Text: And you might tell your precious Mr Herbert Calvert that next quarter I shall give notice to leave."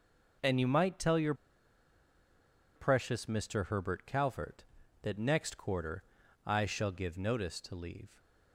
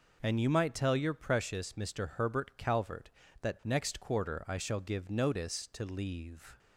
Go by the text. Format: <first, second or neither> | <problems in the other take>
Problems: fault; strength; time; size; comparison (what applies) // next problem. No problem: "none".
second | pauses between "your" and "precious"; strong; at 1.3 s; 1.4 s long // pauses between "quarter" and "I"; at 6.0 s; 0.42 s long